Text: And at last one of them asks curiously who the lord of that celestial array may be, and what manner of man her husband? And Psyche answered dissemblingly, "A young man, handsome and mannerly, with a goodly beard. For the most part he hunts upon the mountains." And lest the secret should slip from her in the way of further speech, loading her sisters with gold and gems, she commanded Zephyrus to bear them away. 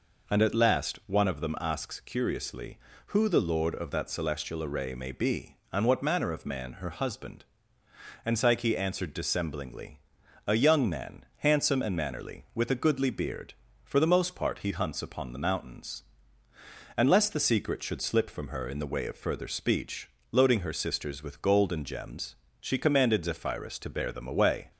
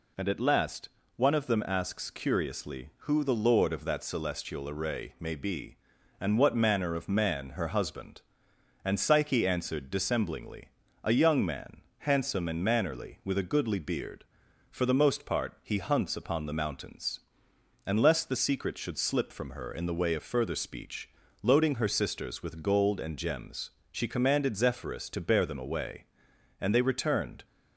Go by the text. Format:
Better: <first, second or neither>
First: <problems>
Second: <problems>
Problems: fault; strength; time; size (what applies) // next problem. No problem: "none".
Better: first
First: none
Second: pauses between "last" and "one"; slight; at 0.8 s; 0.28 s long // goes on to say "And they returned"; noticeable; from 26.5 s on; 0.86 s long